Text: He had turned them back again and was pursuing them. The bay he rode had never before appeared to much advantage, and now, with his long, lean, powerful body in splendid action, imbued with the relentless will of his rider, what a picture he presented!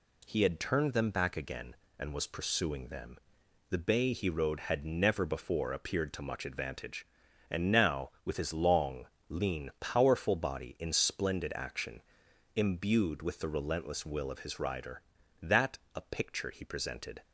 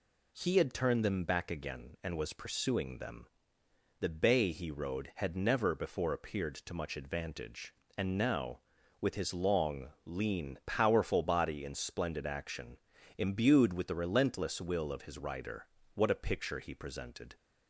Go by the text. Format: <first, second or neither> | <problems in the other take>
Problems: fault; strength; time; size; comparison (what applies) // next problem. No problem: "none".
second | says "that" for "what"; at 15.4 s